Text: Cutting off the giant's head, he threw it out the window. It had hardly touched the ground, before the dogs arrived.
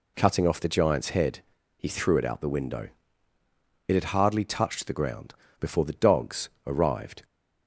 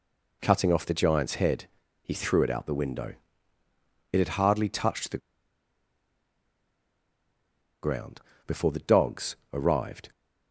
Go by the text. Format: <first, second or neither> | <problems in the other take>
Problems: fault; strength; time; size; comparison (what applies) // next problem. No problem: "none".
first | pauses between "the" and "ground"; strong; at 5.1 s; 2.6 s long // pauses between "dogs" and "arrived"; slight; at 9.3 s; 0.16 s long; slight in the first